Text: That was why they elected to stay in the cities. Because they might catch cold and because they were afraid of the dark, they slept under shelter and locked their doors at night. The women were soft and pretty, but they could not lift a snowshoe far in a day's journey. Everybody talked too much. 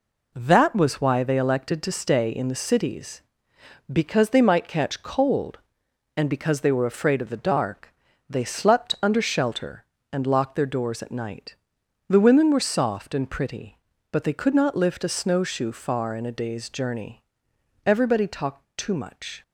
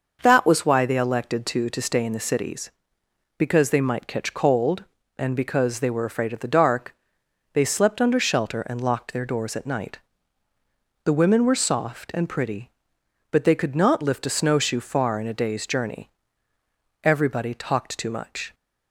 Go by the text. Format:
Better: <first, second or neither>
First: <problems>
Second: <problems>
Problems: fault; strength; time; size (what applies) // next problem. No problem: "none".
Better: first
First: none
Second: starts louder than the rest; noticeable; until 1.2 s; 6 dB // says "to" twice; at 1.6 s